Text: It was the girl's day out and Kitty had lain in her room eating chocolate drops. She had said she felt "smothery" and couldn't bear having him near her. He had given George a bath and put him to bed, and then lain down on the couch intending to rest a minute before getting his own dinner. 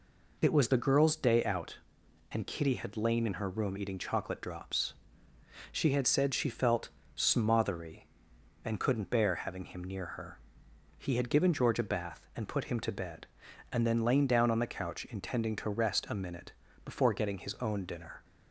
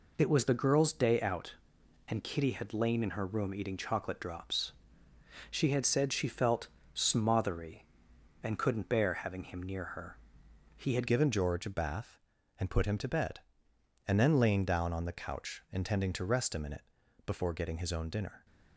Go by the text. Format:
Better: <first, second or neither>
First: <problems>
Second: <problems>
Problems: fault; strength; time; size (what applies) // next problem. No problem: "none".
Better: first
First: pauses between "felt" and "smothery"; slight; at 6.8 s; 0.26 s long // pauses between "minute" and "before"; slight; at 16.5 s; 0.32 s long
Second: pauses between "felt" and "smothery"; slight; at 6.6 s; 0.26 s long // changes voice at "given"; from 11.0 s on; 7.4 s long // pauses between "minute" and "before"; at 16.8 s; 0.42 s long